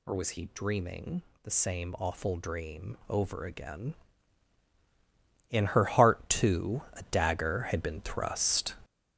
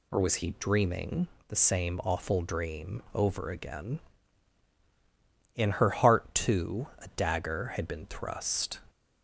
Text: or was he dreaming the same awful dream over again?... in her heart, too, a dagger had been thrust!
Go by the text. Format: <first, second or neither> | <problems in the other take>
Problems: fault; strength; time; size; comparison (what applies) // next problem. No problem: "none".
second | gets louder; strong; throughout; 7.5 dB // pauses between "dreaming" and "the"; slight; at 1.2 s; 0.22 s long; slight in the second